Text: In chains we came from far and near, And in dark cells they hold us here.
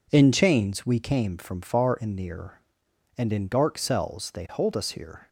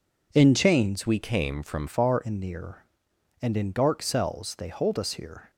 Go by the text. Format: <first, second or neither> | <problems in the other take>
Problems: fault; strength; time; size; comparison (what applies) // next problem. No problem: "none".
first | changes voice from "we" to "from"; from 1.0 to 1.8 s; 0.8 s long